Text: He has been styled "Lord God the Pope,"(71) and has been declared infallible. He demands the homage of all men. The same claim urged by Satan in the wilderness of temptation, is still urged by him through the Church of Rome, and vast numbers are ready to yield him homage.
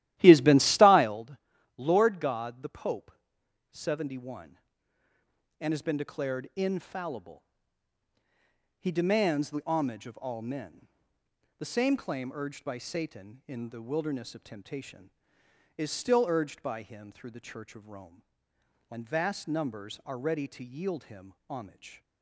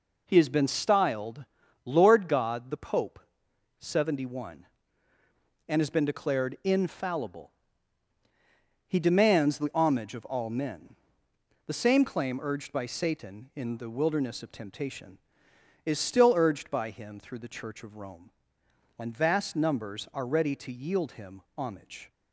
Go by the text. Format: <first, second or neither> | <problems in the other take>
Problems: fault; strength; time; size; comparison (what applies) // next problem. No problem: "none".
second | starts louder than the rest; strong; until 1.2 s; 14.5 dB // pauses between "styled" and "Lord"; at 1.3 s; 0.40 s long; also in the second